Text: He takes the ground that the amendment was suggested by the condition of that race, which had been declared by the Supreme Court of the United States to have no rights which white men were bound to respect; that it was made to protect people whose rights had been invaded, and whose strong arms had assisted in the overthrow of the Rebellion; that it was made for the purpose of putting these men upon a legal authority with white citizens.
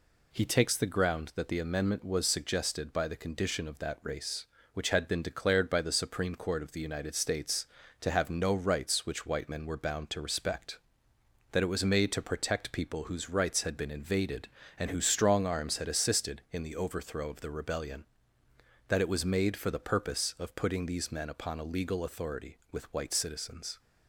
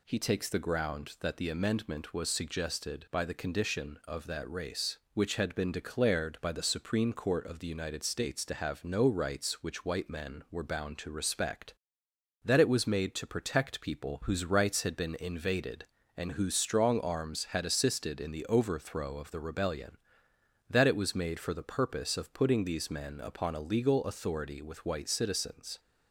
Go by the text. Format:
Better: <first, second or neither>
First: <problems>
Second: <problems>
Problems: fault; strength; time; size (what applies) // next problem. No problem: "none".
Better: neither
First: none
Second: none